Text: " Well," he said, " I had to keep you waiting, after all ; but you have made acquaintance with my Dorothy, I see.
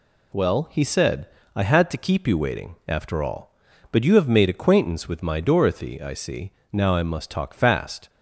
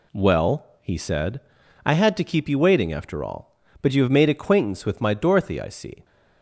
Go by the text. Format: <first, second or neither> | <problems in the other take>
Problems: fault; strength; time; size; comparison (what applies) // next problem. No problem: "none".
second | goes on to say "Now I must talk fast"; from 6.7 s on; 1.3 s long